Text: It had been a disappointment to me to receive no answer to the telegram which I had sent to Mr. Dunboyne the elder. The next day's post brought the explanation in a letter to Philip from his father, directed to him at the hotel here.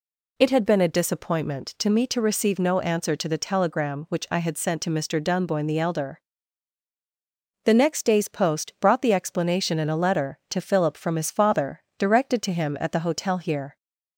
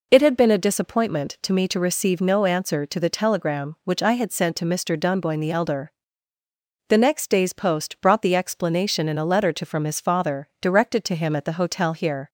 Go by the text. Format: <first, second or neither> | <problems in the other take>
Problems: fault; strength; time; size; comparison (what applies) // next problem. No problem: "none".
first | skips "Philip"; at 9.6 s